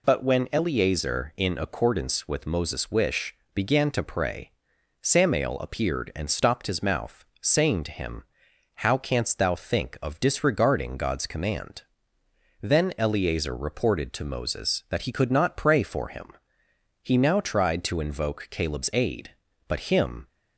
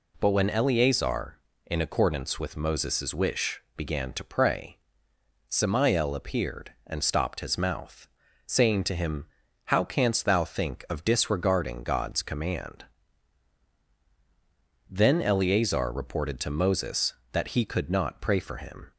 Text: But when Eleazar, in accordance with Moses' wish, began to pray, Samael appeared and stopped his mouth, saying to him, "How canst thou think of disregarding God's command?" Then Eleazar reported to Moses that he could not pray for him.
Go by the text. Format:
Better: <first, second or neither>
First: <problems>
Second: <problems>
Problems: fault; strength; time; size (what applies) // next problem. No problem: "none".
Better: second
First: goes on to say "He now tried to invoke Caleb's aid but him"; strong; from 17.0 s on; 3.2 s long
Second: none